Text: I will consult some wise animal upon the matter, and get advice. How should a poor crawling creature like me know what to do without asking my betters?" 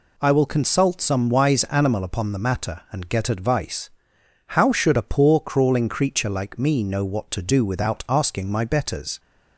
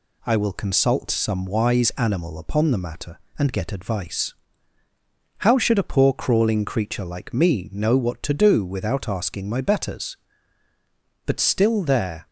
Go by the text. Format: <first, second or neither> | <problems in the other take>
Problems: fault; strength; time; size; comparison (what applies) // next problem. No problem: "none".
first | goes on to say "But still there"; noticeable; from 11.2 s on; 1.0 s long